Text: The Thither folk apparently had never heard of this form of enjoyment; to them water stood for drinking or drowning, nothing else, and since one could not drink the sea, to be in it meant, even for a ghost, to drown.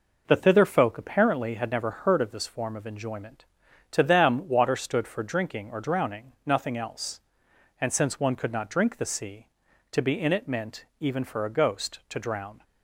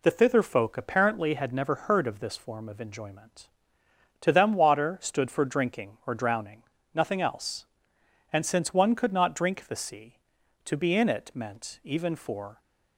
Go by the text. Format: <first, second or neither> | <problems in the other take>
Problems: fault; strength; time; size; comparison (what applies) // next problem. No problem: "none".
first | stops before "a ghost to drown"; at 12.6 s